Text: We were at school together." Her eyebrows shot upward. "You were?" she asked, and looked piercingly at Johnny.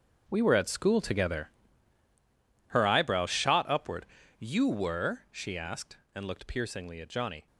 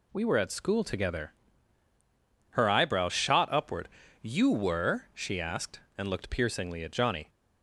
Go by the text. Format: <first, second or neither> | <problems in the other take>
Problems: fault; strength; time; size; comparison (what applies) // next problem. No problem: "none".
second | gets quieter; strong; throughout; 12.5 dB